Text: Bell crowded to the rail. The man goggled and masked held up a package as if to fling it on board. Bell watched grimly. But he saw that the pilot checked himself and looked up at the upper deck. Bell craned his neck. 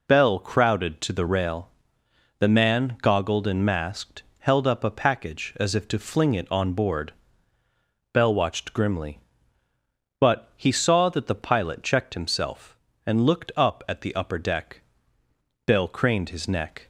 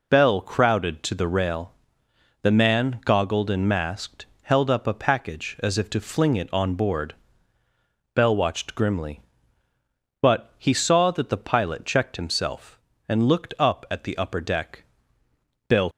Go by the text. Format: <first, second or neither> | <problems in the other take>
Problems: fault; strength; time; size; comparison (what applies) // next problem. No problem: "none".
first | pauses between "masked" and "held"; slight; at 4.2 s; 0.16 s long; slight in the first // stops before "craned his neck"; at 15.9 s